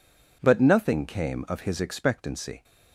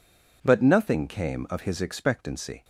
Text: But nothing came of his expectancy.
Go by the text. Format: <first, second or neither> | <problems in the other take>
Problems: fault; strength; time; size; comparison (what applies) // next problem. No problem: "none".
neither | none